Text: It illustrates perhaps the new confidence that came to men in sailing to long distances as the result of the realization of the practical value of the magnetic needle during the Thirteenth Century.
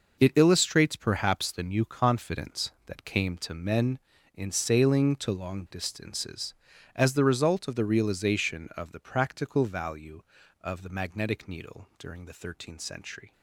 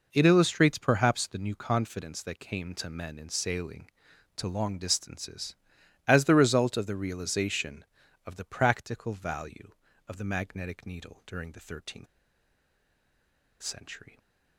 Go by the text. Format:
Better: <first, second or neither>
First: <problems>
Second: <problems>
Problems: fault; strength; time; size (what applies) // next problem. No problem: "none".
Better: first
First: none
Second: pauses between "Thirteenth" and "Century"; strong; at 12.0 s; 1.5 s long